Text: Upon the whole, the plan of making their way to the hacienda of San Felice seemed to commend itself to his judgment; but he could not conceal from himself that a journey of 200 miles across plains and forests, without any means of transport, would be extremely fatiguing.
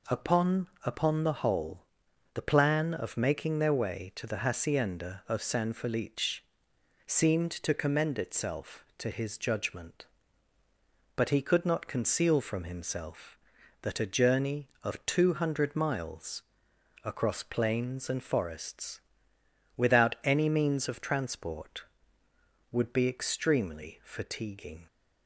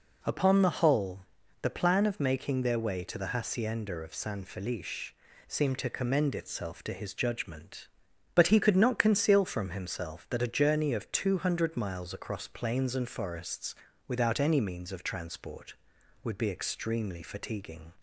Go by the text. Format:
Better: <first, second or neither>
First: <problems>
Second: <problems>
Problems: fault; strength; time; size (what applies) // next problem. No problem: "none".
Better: second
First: says "Upon" twice; at 0.8 s // pauses between "Felice" and "seemed"; noticeable; at 6.4 s; 0.66 s long // pauses between "miles" and "across"; noticeable; at 16.4 s; 0.60 s long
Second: pauses between "Felice" and "seemed"; slight; at 5.1 s; 0.34 s long